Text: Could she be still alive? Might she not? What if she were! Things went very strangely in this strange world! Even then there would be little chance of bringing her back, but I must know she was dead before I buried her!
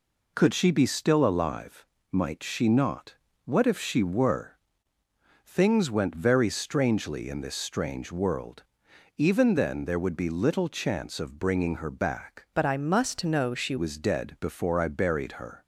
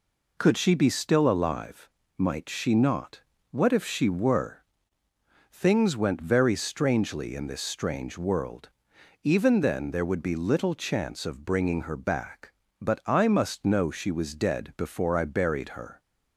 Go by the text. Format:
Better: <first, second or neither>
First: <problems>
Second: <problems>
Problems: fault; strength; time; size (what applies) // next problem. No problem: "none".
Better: second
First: changes voice from "but" to "she"; from 12.5 to 13.7 s; 1.2 s long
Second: none